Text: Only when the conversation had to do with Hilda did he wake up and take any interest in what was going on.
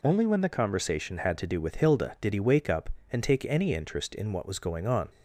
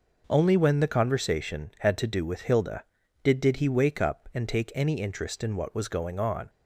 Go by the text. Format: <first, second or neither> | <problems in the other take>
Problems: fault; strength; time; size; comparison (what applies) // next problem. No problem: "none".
first | says "did" twice; at 3.3 s